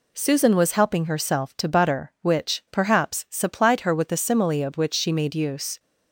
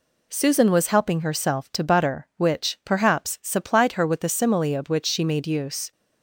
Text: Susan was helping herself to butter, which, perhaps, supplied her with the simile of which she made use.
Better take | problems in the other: neither | none

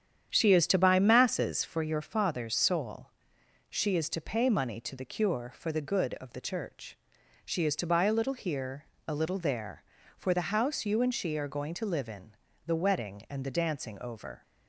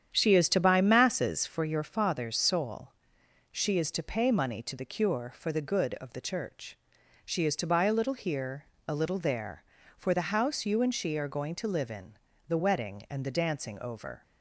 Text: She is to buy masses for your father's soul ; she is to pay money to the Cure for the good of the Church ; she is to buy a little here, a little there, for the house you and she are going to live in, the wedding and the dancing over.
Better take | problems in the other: neither | starts louder than the rest; strong; the same in both

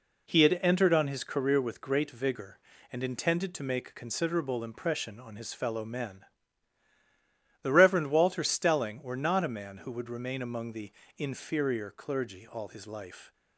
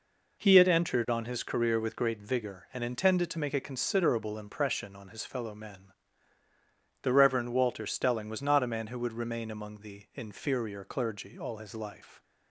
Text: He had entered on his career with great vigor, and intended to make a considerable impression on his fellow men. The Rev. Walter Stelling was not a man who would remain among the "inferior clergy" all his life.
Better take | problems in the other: second | says "were" for "was"; at 9.0 s // pauses between "the" and "inferior"; slight; at 10.9 s; 0.28 s long

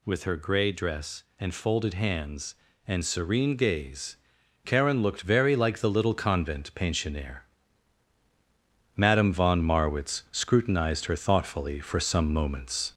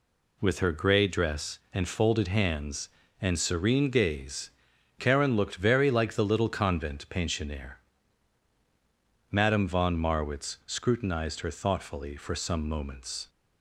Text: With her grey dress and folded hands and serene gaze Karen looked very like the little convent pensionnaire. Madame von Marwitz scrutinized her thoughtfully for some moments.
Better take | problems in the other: second | gets louder; slight; throughout; 2.5 dB // pauses between "gaze" and "Karen"; noticeable; at 4.1 s; 0.48 s long; noticeable in the second

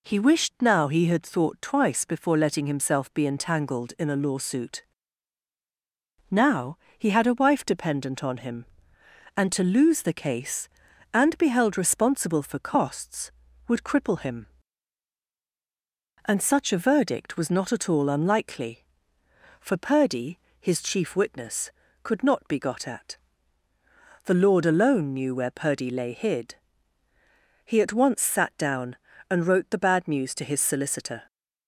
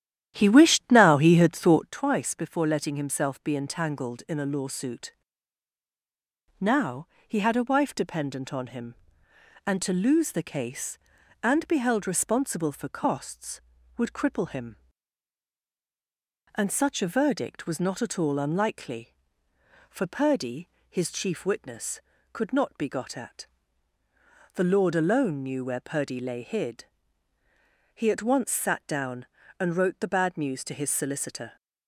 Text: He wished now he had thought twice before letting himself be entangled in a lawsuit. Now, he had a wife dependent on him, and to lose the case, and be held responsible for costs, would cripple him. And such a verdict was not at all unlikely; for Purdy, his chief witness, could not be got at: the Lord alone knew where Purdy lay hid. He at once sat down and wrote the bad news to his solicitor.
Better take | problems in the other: first | starts louder than the rest; strong; until 1.9 s; 11.5 dB

